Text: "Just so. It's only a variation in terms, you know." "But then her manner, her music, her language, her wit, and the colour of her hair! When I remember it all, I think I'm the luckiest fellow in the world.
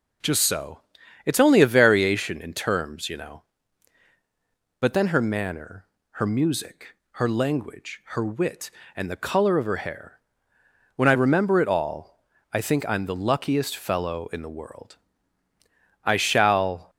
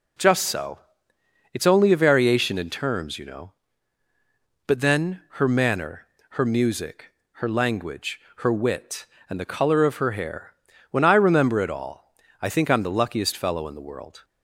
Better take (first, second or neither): second